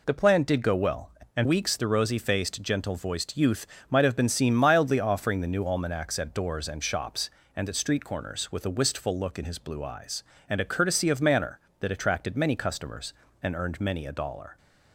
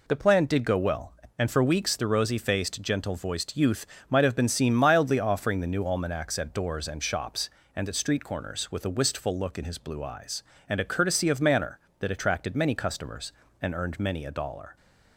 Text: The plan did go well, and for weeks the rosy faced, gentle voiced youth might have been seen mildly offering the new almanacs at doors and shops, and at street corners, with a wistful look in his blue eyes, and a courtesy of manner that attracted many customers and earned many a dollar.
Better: second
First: skips "for"; at 1.4 s // pauses between "youth" and "might"; slight; at 3.6 s; 0.24 s long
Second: pauses between "youth" and "might"; slight; at 3.8 s; 0.24 s long

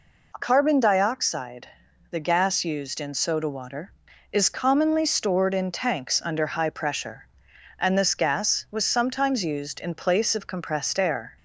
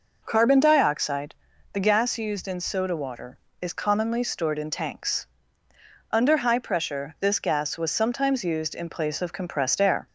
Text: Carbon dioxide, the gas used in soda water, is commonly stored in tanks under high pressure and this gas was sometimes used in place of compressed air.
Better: first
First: none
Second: pauses between "tanks" and "under"; noticeable; at 5.2 s; 0.86 s long // skips "and"; at 7.1 s

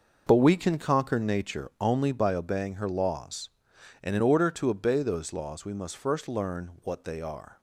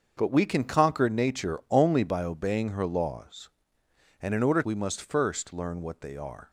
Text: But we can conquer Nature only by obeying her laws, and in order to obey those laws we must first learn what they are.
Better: first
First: none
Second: starts louder than the rest; until 1.1 s; 6.5 dB // skips "to obey those laws"; at 4.6 s

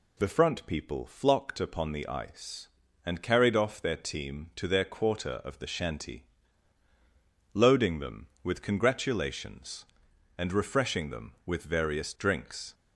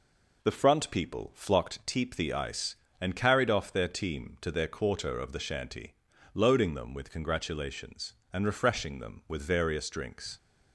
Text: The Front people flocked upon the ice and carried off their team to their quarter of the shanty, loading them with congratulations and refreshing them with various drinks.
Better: first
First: none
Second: says "teep" for "upon"; at 1.8 s

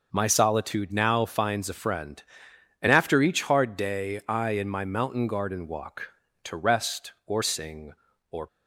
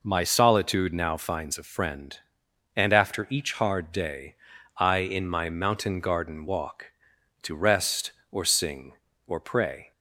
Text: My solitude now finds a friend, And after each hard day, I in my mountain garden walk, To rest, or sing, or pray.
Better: second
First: stops before "pray"; at 8.4 s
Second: none

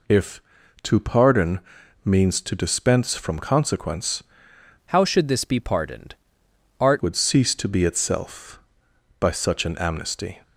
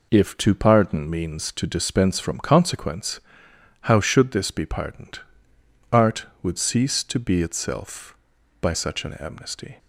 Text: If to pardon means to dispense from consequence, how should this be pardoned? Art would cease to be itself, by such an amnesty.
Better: second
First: pauses between "pardon" and "means"; at 1.5 s; 0.44 s long // changes voice from "how" to "Art"; from 4.8 to 7.0 s; 2.2 s long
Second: none

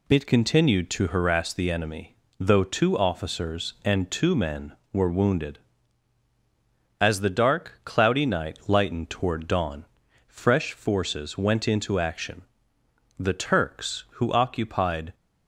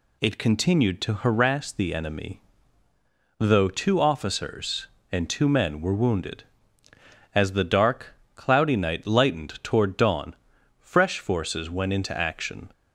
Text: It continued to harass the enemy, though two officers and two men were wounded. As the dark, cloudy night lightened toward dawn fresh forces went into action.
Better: second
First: pauses between "dawn" and "fresh"; at 9.8 s; 0.44 s long // goes on to say "The Turks who occupied"; strong; from 13.1 s on; 1.9 s long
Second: pauses between "dawn" and "fresh"; noticeable; at 10.3 s; 0.46 s long

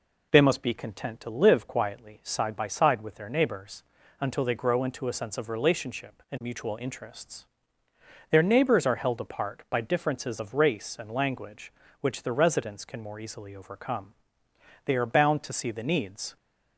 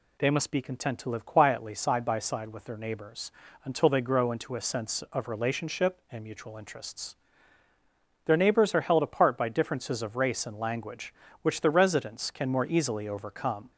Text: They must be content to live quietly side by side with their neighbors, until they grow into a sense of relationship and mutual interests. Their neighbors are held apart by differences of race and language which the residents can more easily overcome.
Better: second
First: goes on to say "They are bound to see the needs"; from 14.8 s on; 1.5 s long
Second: none

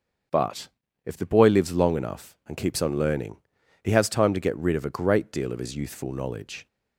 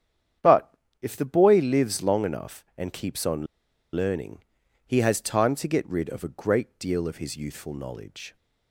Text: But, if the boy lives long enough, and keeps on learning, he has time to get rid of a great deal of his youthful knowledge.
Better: first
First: starts louder than the rest; strong; until 1.7 s; 7.5 dB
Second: starts louder than the rest; strong; until 1.6 s; 9 dB // pauses between "on" and "learning"; noticeable; at 3.4 s; 0.49 s long

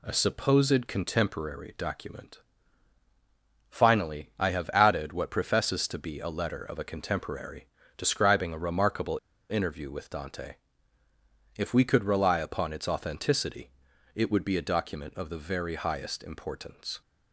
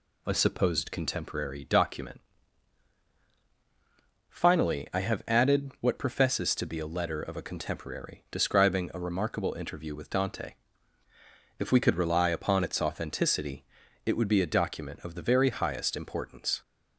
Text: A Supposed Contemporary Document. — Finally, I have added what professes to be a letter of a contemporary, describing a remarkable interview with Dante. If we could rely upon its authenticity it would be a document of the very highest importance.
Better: second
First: pauses between "remarkable" and "interview"; slight; at 9.1 s; 0.31 s long // pauses between "authenticity" and "it"; at 13.7 s; 0.44 s long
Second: pauses between "authenticity" and "it"; at 13.6 s; 0.42 s long

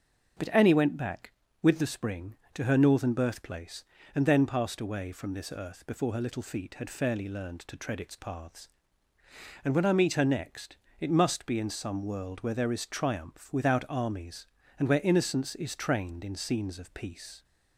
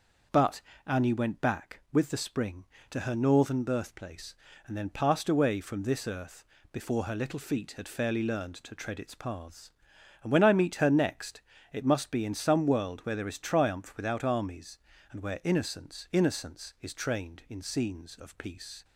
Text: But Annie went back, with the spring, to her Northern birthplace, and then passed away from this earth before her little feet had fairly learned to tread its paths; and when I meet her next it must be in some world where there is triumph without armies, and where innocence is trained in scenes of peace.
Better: first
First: starts louder than the rest; until 1.7 s; 6.5 dB // pauses between "next" and "it"; slight; at 10.7 s; 0.22 s long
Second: starts louder than the rest; until 1.5 s; 6 dB // pauses between "But" and "Annie"; slight; at 0.6 s; 0.24 s long // pauses between "earth" and "before"; slight; at 6.4 s; 0.30 s long // pauses between "next" and "it"; slight; at 11.4 s; 0.30 s long // says "innocence" twice; at 16.1 s

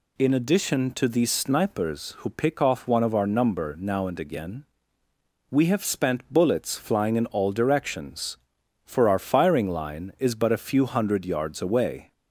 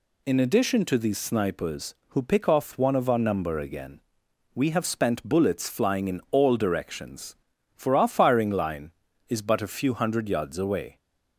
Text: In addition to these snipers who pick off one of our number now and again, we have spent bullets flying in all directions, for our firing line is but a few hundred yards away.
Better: first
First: none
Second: skips "now and"; at 3.5 s

